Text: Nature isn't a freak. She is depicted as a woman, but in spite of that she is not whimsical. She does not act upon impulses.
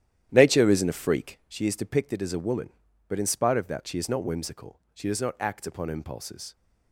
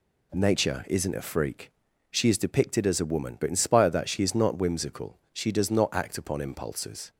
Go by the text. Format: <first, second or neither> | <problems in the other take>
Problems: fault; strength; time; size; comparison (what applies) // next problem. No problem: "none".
second | starts louder than the rest; strong; until 1.6 s; 11.5 dB